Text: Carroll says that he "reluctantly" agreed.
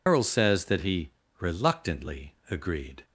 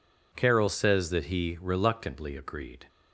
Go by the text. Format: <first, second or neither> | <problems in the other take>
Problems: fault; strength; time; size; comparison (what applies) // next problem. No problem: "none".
second | loses the start of "Carroll"; at 0.0 s; 145 ms // pauses between "he" and "reluctantly"; slight; at 1.1 s; 0.28 s long